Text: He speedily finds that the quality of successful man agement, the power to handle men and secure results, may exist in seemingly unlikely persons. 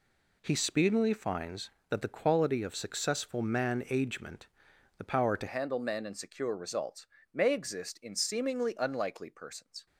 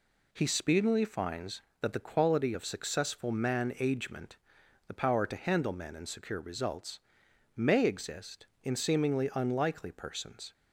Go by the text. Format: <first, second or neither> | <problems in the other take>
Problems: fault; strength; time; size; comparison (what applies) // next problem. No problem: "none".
second | changes voice at "handle"; from 5.4 s on; 4.4 s long